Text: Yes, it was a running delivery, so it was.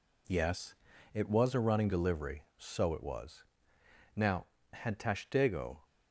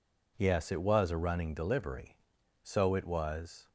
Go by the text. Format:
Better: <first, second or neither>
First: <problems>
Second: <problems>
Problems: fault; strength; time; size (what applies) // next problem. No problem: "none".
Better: second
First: goes on to say "Now had Tashtego"; from 4.1 s on; 1.6 s long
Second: none